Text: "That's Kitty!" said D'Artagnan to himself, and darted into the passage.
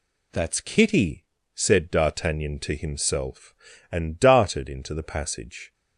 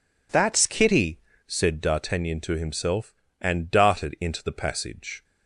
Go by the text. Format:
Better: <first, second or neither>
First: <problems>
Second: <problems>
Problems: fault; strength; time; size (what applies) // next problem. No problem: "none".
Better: neither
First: none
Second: none